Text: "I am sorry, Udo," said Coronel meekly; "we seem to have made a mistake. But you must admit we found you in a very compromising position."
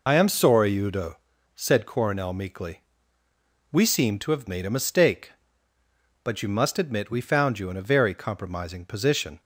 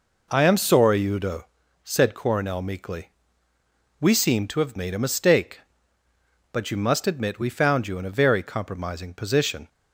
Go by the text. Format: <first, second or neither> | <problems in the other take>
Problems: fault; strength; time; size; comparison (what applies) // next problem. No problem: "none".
second | loses the start of "I"; at 0.0 s; 50 ms